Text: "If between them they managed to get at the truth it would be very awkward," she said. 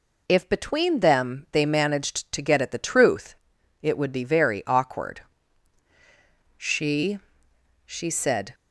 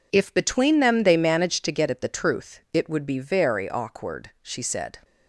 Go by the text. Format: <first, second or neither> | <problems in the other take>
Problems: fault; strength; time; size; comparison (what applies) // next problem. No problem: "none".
second | pauses between "truth" and "it"; noticeable; at 3.3 s; 0.48 s long // says "she" twice; at 7.8 s